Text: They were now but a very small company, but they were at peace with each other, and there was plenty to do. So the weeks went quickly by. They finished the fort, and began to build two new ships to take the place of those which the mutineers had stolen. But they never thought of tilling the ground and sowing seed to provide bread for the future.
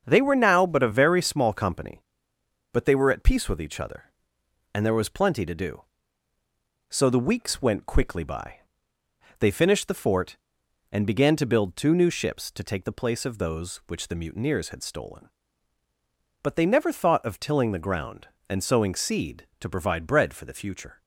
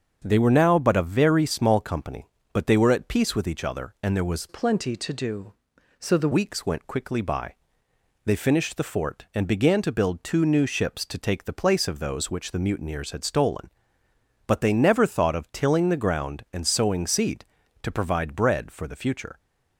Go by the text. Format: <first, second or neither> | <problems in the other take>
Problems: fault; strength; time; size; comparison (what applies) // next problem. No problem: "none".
first | starts louder than the rest; until 1.2 s; 7 dB; strong in the first // changes voice from "plenty" to "the"; from 4.4 to 6.2 s; 1.8 s long